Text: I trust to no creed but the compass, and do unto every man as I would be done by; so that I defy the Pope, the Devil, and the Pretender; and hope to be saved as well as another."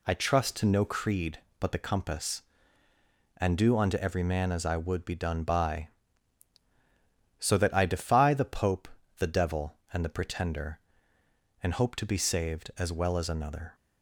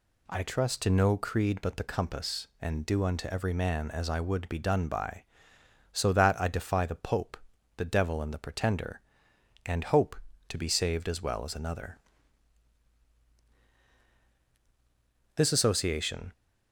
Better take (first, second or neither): first